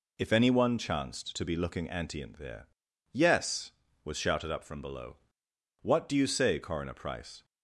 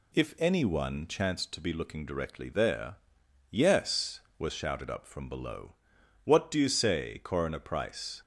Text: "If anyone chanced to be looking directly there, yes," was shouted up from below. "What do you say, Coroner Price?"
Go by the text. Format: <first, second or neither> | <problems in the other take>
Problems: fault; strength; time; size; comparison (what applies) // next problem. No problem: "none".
second | says "antient" for "directly"; at 1.8 s